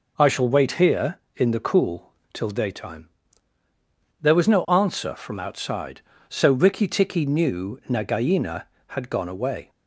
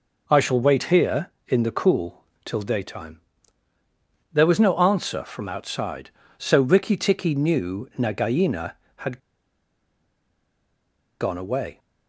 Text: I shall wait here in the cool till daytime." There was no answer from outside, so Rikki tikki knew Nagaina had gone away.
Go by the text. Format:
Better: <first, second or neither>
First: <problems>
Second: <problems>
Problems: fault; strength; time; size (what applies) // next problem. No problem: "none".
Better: first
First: pauses between "cool" and "till"; slight; at 2.1 s; 0.18 s long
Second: pauses between "cool" and "till"; slight; at 2.2 s; 0.18 s long // pauses between "had" and "gone"; strong; at 9.1 s; 2.0 s long